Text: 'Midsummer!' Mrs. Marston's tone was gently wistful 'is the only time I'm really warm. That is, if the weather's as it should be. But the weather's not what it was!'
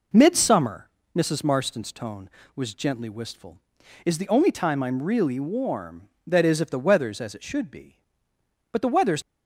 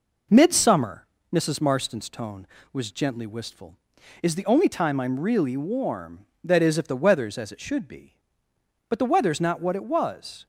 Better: second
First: stops before "not what it was"; at 9.2 s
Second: none

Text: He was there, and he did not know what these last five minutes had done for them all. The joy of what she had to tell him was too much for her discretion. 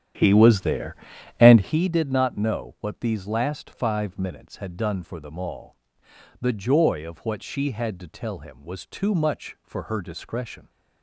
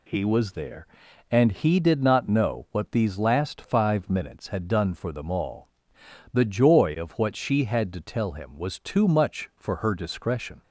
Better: second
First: starts louder than the rest; strong; until 1.8 s; 10 dB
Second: none

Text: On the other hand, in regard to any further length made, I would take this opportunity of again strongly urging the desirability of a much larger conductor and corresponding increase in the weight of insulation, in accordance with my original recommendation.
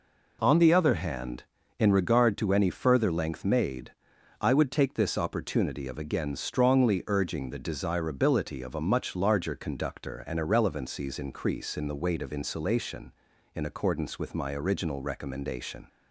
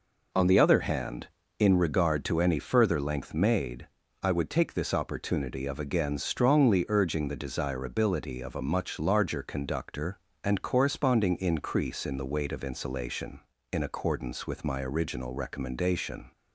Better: second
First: says "irrelevancies" for "corresponding"; at 10.3 s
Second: none

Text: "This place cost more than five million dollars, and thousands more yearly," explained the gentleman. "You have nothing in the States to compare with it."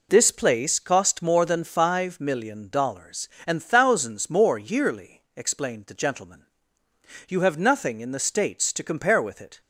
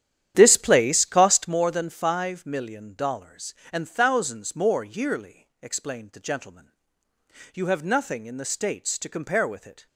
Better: first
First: none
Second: starts louder than the rest; strong; until 1.6 s; 10.5 dB

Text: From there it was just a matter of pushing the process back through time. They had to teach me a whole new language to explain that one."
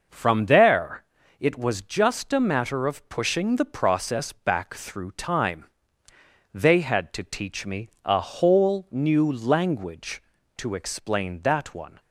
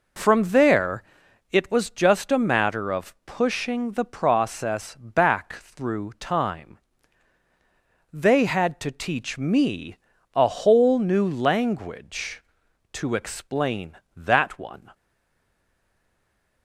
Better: first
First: pauses between "there" and "it"; slight; at 1.0 s; 0.34 s long // pauses between "me" and "a"; slight; at 7.8 s; 0.16 s long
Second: pauses between "there" and "it"; noticeable; at 1.0 s; 0.48 s long // pauses between "me" and "a"; slight; at 9.9 s; 0.36 s long // stays silent after the last word; noticeable; from 14.9 s on; 1.7 s long

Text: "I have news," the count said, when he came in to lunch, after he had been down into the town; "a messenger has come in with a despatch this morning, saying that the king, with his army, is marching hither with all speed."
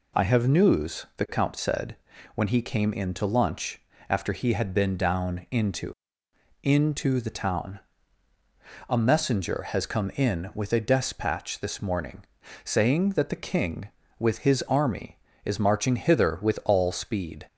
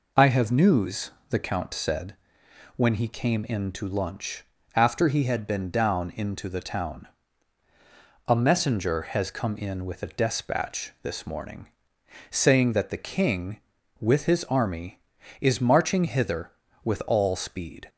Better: second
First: says "into" twice; at 6.6 s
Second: none

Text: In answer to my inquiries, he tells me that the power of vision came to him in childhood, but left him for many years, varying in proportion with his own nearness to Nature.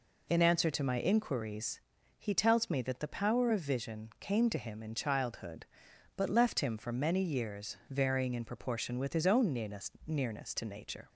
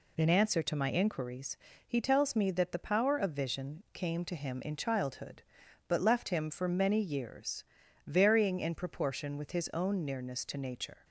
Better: second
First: says "nearness" twice; at 10.0 s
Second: none

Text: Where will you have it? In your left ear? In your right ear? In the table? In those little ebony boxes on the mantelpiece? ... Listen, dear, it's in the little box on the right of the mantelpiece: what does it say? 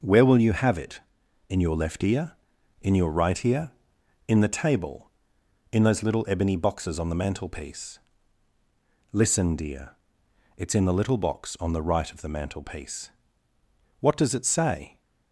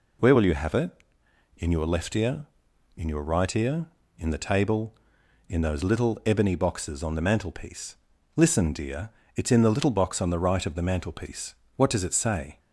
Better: neither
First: none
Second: none

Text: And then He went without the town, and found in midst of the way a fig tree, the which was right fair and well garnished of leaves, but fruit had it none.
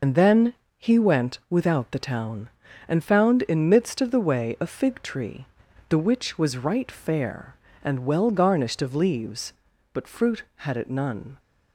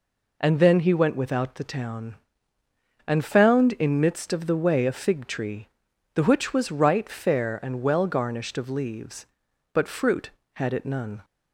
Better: second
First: loses the start of "And"; at 0.0 s; 65 ms // pauses between "then" and "He"; slight; at 0.5 s; 0.24 s long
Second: none

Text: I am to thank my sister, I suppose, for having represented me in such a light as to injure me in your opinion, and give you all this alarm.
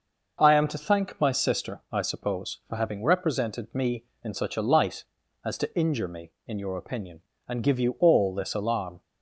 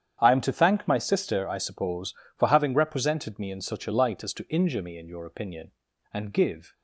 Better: first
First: none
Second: starts louder than the rest; strong; until 1.2 s; 9 dB // stops before "you all this alarm"; at 6.7 s

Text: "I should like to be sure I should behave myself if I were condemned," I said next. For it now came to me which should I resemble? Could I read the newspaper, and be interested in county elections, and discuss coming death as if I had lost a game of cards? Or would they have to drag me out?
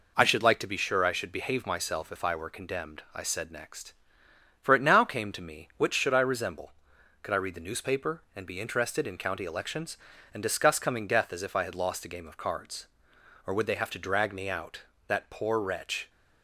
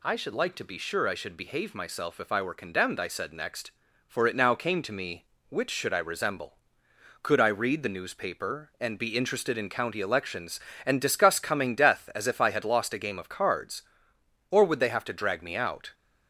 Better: second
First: goes on to say "That poor wretch"; noticeable; from 15.0 s on; 1.0 s long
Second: none

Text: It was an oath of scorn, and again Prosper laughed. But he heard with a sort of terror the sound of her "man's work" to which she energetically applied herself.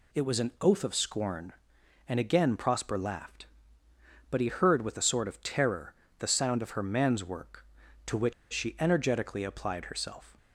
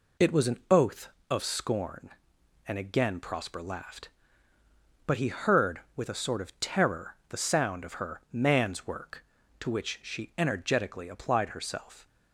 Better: second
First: pauses between "terror" and "the"; slight; at 5.9 s; 0.26 s long // pauses between "which" and "she"; slight; at 8.3 s; 0.19 s long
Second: none

